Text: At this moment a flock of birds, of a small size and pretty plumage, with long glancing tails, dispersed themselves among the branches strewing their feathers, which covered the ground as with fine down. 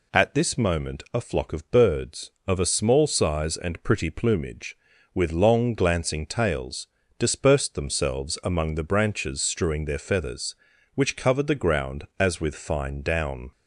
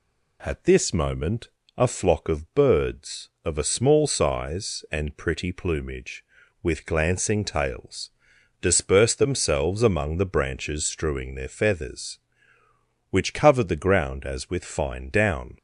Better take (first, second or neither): first